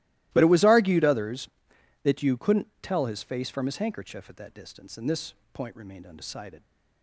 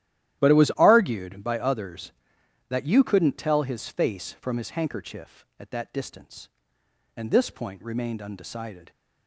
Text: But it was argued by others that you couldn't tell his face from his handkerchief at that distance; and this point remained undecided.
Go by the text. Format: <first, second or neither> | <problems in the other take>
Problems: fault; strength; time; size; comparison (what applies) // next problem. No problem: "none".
second | starts louder than the rest; strong; until 1.3 s; 17 dB; strong in the second // skips "by"; at 1.0 s // pauses between "this" and "point"; slight; at 5.3 s; 0.18 s long